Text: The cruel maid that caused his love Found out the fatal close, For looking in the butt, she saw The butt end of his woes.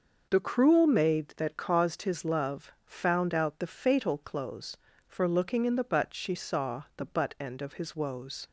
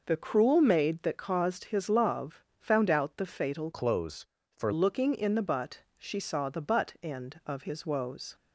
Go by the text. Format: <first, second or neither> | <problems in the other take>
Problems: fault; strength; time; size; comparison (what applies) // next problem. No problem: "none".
first | pauses between "love" and "Found"; slight; at 2.4 s; 0.20 s long // changes voice from "close" to "For"; from 3.7 to 4.7 s; 1.0 s long